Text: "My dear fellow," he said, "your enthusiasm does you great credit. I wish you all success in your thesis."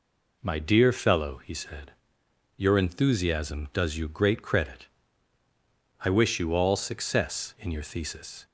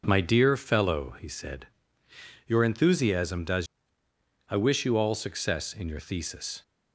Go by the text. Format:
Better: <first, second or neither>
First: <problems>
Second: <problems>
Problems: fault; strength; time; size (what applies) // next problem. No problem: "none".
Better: first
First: none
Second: skips "you great credit"; at 4.0 s